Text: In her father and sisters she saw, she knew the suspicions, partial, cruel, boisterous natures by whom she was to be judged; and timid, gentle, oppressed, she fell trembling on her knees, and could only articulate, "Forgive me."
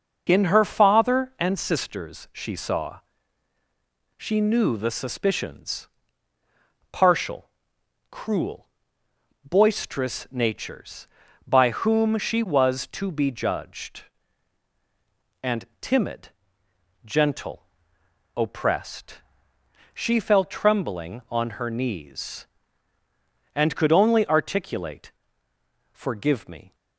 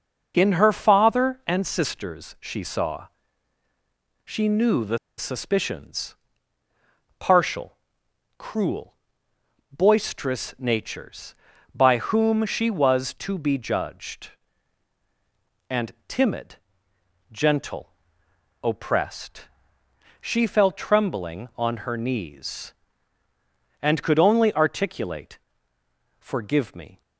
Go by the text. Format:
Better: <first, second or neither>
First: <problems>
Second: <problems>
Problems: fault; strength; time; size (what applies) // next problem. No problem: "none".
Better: first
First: pauses between "and" and "timid"; slight; at 15.6 s; 0.16 s long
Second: pauses between "the" and "suspicions"; slight; at 4.9 s; 0.20 s long // pauses between "and" and "timid"; slight; at 15.9 s; 0.16 s long